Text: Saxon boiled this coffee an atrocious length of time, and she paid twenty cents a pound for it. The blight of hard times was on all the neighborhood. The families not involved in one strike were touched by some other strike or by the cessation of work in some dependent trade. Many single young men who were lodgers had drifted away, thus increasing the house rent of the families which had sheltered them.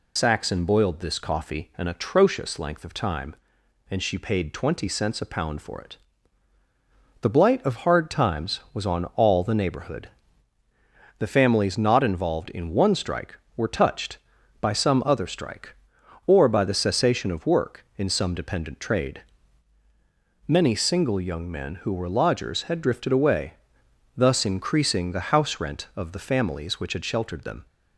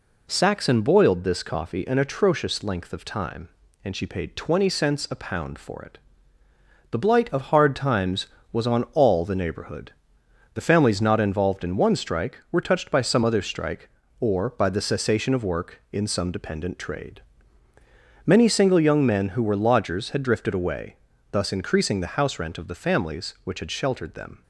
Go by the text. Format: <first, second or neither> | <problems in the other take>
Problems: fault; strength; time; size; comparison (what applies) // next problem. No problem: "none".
second | loses the start of "Saxon"; at 0.1 s; 55 ms